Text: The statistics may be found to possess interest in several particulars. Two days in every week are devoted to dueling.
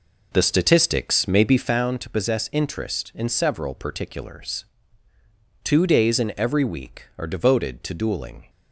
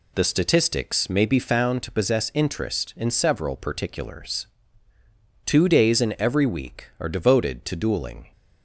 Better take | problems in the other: second | starts louder than the rest; noticeable; until 1.7 s; 4.5 dB

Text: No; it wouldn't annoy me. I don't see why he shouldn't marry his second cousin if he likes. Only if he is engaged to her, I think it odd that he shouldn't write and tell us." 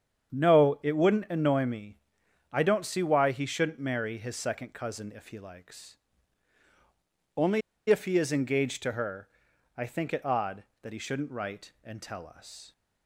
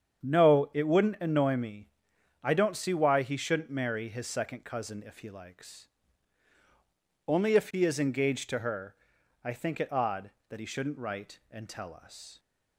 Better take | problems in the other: second | starts louder than the rest; strong; until 1.4 s; 8.5 dB; strong in the second // pauses between "Only" and "if"; slight; at 7.6 s; 0.29 s long

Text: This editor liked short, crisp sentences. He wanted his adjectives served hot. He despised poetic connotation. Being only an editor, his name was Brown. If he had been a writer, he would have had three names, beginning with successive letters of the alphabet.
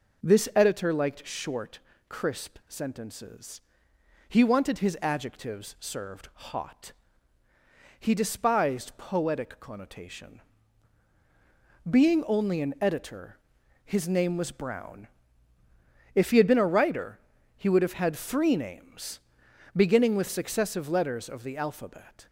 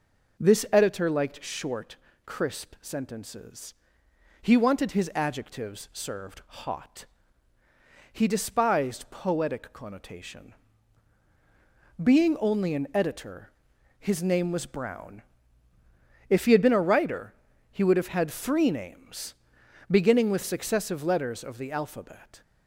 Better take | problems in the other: neither | none

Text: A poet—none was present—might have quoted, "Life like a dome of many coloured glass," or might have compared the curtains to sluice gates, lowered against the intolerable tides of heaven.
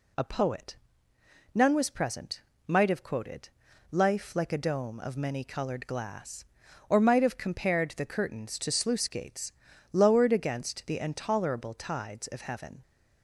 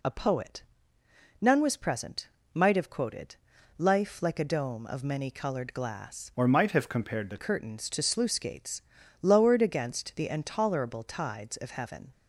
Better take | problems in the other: first | changes voice from "or" to "the"; from 6.3 to 7.3 s; 1.0 s long

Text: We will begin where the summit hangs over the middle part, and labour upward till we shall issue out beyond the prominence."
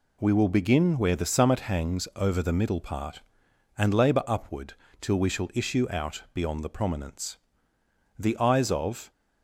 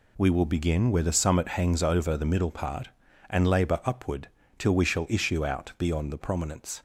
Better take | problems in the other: second | pauses between "upward" and "till"; slight; at 4.7 s; 0.26 s long; slight in the second // goes on to say "The eyes of"; noticeable; from 8.1 s on; 0.94 s long

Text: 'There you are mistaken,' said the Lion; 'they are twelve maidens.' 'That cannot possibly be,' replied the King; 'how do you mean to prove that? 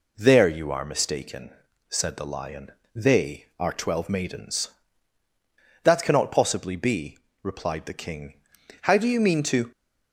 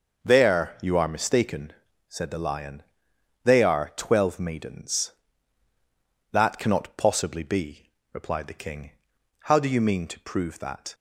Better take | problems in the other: second | stops before "prove that"; at 9.7 s

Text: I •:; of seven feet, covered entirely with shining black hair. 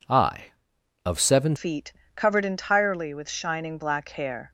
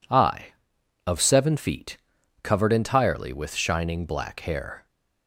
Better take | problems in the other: second | changes voice at "feet"; from 1.5 s on; 3.0 s long

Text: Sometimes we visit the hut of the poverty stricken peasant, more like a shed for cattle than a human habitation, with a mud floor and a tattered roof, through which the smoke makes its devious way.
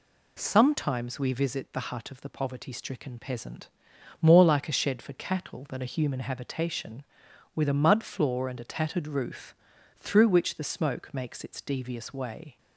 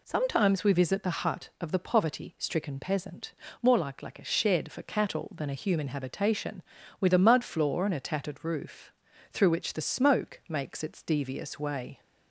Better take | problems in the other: first | says "like" twice; at 4.0 s

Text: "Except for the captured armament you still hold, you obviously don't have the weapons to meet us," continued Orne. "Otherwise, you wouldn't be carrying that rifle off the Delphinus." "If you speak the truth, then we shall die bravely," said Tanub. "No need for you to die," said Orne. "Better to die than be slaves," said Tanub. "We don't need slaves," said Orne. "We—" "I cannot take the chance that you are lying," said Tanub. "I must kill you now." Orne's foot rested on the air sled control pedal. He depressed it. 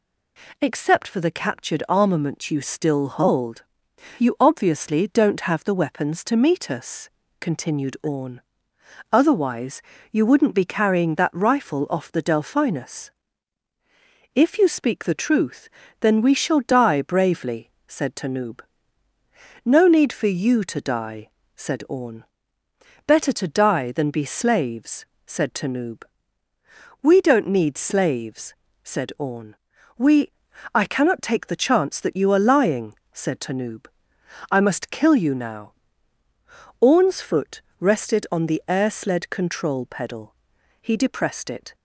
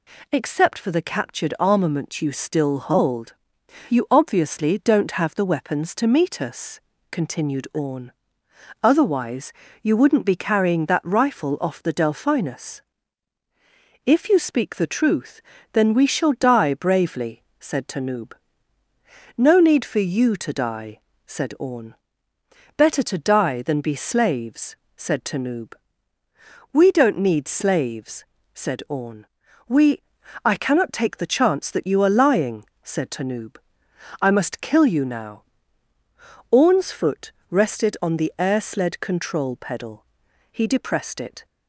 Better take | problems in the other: neither | pauses between "foot" and "rested"; slight; the same in both

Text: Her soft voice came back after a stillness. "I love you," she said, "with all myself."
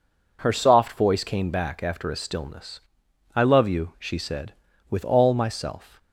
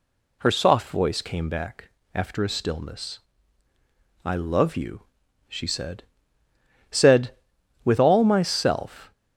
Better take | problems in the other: first | pauses between "back" and "after"; slight; at 1.8 s; 0.24 s long // says "said" twice; at 6.8 s

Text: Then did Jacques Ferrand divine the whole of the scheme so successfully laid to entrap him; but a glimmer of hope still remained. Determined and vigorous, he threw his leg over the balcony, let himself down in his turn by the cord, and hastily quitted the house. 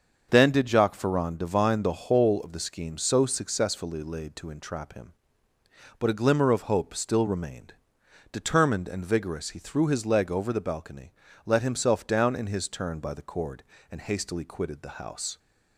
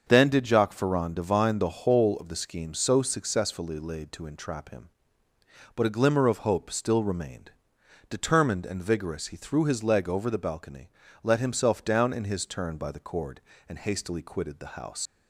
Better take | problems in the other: first | starts louder than the rest; until 1.0 s; 6.5 dB; also in the first // leaves "house" unfinished; at 15.0 s; 105 ms

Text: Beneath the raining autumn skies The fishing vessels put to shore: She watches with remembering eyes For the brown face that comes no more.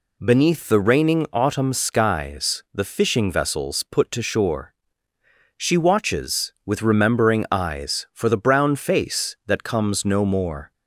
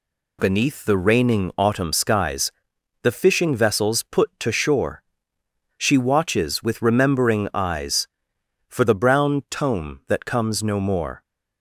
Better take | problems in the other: first | pauses between "skies" and "The"; noticeable; at 2.4 s; 0.52 s long // says "tome" for "face"; at 9.4 s

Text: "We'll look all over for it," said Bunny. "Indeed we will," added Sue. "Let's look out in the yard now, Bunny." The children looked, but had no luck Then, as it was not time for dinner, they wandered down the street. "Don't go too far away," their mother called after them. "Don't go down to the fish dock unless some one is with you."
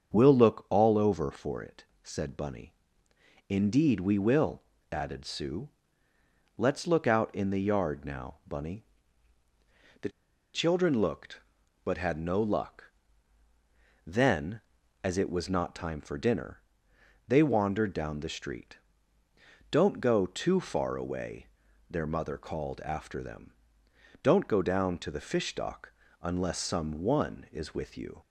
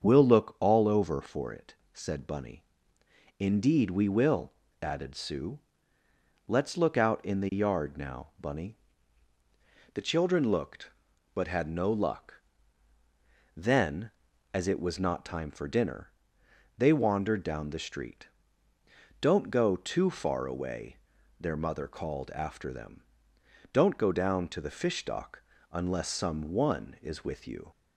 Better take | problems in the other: second | starts louder than the rest; until 1.1 s; 7 dB; also in the second // pauses between "The" and "children"; at 10.1 s; 0.43 s long // pauses between "luck" and "Then"; at 12.8 s; 1.2 s long; also in the second // pauses between "dock" and "unless"; slight; at 25.9 s; 0.30 s long; slight in the second

